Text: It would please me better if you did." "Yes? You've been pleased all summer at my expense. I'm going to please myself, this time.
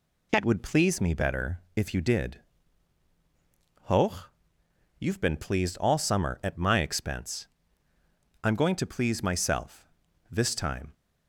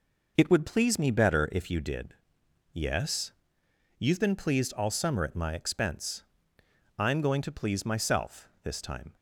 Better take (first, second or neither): second